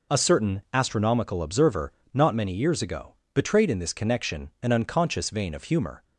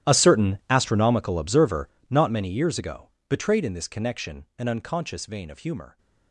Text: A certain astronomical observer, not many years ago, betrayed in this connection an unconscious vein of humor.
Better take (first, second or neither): first